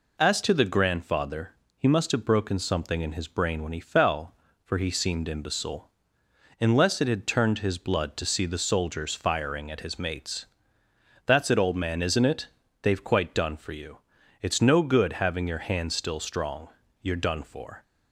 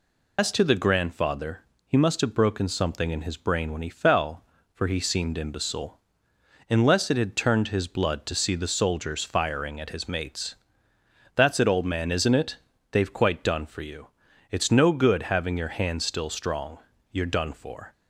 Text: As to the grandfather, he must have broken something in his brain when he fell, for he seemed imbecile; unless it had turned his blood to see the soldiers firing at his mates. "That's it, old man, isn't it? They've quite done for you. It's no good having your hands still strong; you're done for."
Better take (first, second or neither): first